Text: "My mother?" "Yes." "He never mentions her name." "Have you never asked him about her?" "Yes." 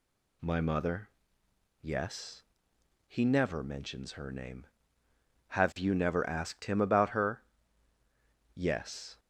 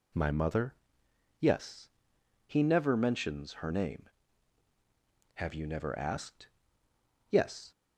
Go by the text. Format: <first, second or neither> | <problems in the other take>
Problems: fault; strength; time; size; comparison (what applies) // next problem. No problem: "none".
first | skips "him about her"; at 6.8 s